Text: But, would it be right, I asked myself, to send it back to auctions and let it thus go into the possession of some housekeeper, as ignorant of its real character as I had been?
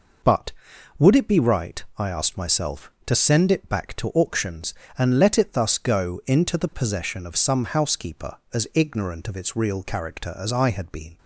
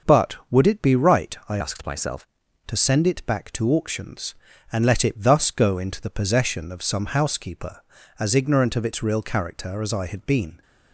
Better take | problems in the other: first | starts louder than the rest; until 1.2 s; 6.5 dB // changes voice from "asked" to "myself"; from 1.6 to 2.2 s; 0.6 s long

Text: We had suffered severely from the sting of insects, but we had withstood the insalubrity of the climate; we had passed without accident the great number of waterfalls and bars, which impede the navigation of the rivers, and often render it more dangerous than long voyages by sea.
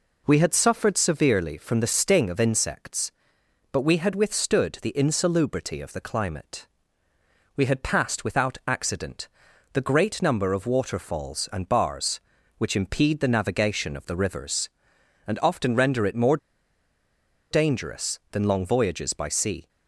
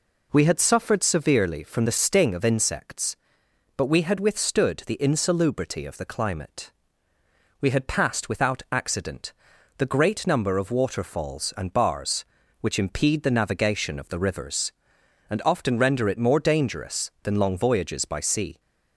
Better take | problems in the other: second | pauses between "accident" and "the"; at 9.2 s; 0.44 s long; also in the second // pauses between "more" and "dangerous"; at 16.3 s; 1.1 s long

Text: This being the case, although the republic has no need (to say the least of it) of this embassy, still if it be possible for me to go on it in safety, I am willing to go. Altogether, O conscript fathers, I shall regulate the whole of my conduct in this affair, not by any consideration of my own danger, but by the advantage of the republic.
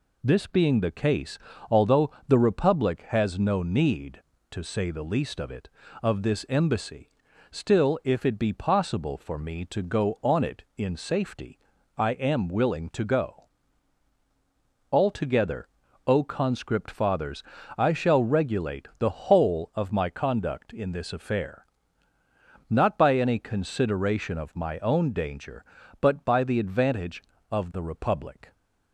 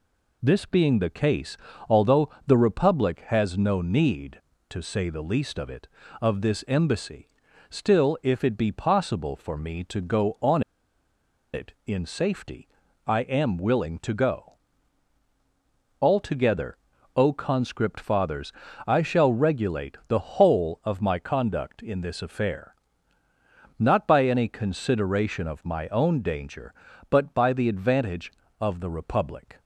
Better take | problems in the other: first | pauses between "although" and "the"; slight; at 2.2 s; 0.16 s long; slight in the first // pauses between "on" and "it"; noticeable; at 10.6 s; 0.91 s long

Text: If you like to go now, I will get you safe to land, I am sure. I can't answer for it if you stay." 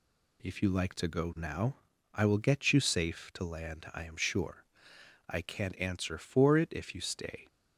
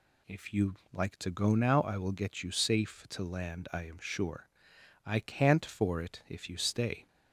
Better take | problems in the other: first | pauses between "you" and "like"; slight; at 0.7 s; 0.16 s long // skips "answer"; at 5.6 s

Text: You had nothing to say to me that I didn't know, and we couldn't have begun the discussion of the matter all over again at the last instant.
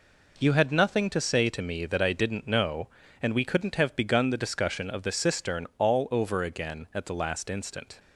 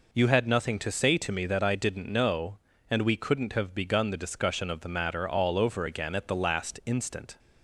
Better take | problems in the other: second | says "cistern" for "matter"; at 5.1 s

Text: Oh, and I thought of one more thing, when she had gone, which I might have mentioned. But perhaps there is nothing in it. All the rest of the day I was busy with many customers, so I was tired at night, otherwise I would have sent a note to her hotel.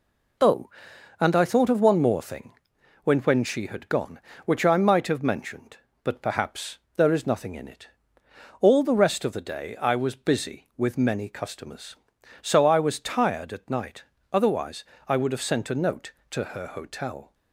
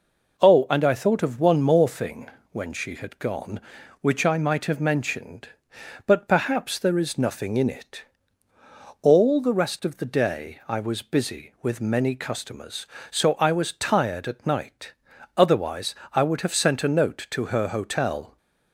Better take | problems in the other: second | says "when" twice; at 3.1 s // pauses between "perhaps" and "there"; slight; at 6.7 s; 0.20 s long // pauses between "otherwise" and "I"; slight; at 14.8 s; 0.24 s long; slight in the second

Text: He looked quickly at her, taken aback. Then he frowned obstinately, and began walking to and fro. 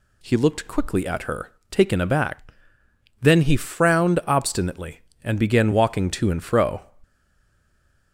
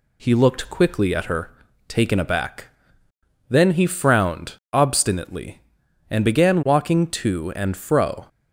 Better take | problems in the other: second | stays silent after the last word; from 7.0 s on; 1.1 s long

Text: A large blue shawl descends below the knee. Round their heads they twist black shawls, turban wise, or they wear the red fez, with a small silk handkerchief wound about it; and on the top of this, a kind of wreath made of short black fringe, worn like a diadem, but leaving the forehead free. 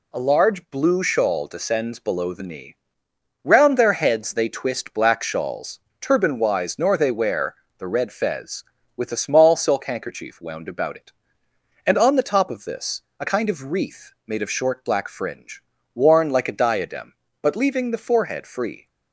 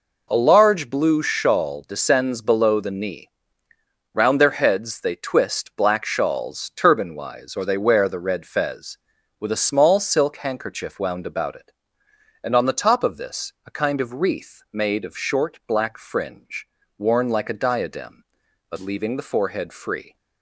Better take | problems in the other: second | says "nor" for "or"; at 6.7 s // pauses between "wear" and "the"; slight; at 7.5 s; 0.22 s long

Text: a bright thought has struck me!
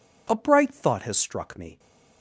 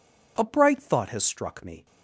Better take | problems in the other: neither | none

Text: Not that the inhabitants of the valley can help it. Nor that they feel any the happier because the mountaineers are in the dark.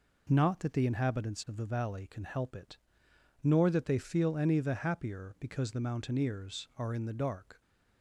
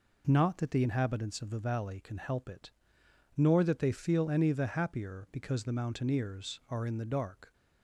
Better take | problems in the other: neither | none

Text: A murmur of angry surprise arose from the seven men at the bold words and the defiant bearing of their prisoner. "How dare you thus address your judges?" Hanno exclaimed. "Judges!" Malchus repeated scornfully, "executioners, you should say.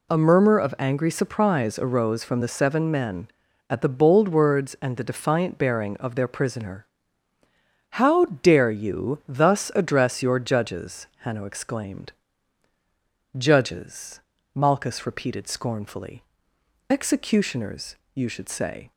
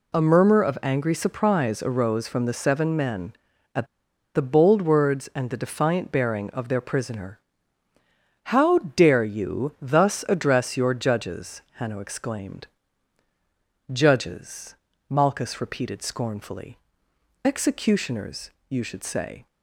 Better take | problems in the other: first | pauses between "at" and "the"; noticeable; at 3.8 s; 0.48 s long

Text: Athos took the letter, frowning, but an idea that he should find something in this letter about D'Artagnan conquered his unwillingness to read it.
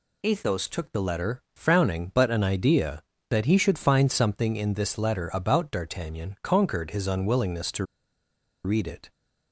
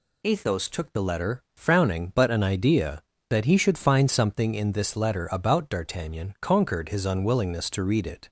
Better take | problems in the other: second | pauses between "to" and "read"; noticeable; at 7.8 s; 0.79 s long

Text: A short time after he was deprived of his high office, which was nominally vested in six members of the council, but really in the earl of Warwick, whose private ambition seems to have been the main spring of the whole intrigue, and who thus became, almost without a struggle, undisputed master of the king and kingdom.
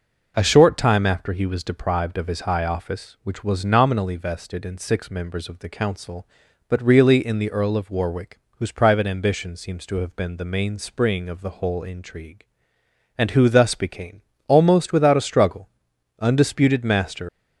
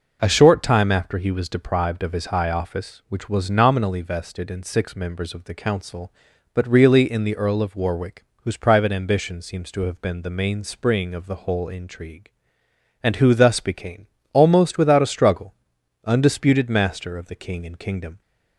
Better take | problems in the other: second | stops before "of the king and kingdom"; at 17.2 s

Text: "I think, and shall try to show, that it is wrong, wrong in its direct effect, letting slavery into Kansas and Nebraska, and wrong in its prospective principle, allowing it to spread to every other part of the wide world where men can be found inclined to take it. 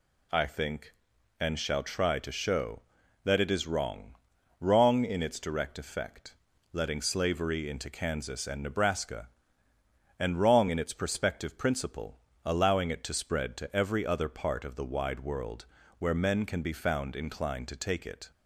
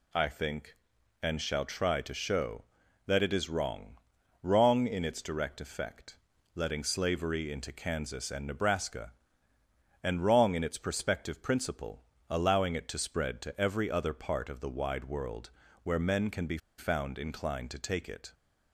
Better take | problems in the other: first | pauses between "world" and "where"; slight; at 15.4 s; 0.34 s long; slight in the first // pauses between "be" and "found"; slight; at 16.5 s; 0.20 s long

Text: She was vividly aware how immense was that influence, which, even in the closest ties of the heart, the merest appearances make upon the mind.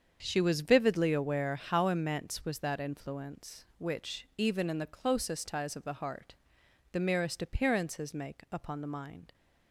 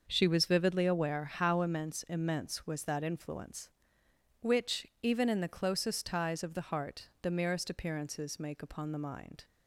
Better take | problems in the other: first | starts louder than the rest; noticeable; until 1.1 s; 6 dB; strong in the first // says "immense" twice; at 2.0 s

